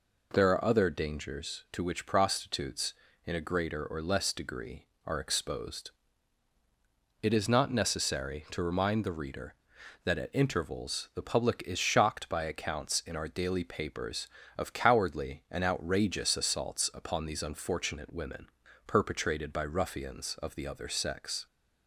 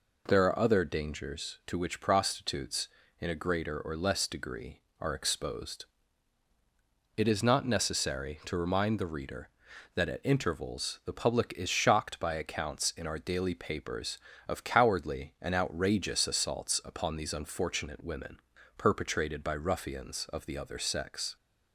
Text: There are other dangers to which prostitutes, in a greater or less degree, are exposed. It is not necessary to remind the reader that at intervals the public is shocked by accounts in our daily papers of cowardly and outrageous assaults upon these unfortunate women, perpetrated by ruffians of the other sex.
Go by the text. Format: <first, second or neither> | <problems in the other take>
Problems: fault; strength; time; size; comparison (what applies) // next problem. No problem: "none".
neither | none